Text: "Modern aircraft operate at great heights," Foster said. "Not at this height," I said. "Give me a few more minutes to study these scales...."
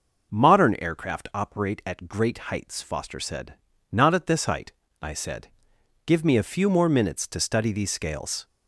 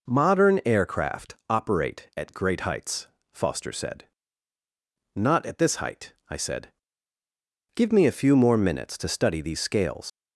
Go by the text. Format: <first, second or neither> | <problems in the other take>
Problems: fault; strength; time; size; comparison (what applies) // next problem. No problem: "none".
first | pauses between "aircraft" and "operate"; slight; at 1.3 s; 0.16 s long // leaves "scales" unfinished; at 10.0 s; 95 ms